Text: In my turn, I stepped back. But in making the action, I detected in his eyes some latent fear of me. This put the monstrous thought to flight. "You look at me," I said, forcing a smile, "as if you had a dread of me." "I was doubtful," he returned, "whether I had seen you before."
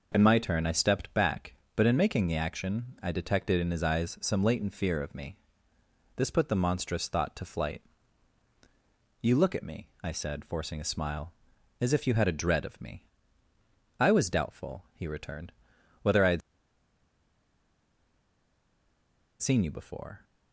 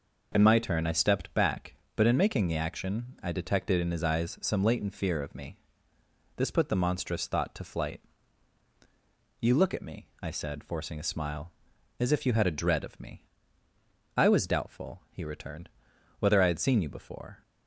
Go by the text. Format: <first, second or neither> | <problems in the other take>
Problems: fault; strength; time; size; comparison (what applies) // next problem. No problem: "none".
second | pauses between "had" and "seen"; strong; at 16.4 s; 3.0 s long